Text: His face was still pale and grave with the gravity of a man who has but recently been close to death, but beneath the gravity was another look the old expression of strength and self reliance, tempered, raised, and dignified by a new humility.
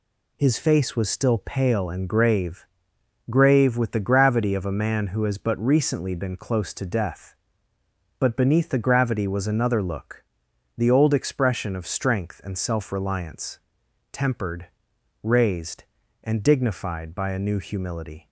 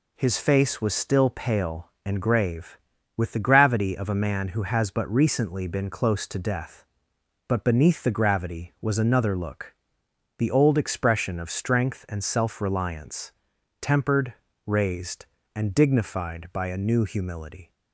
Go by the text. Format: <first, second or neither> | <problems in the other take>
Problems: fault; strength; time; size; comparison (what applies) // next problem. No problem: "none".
second | says "grave" twice; at 3.3 s // pauses between "look" and "the"; noticeable; at 10.2 s; 0.54 s long; noticeable in the second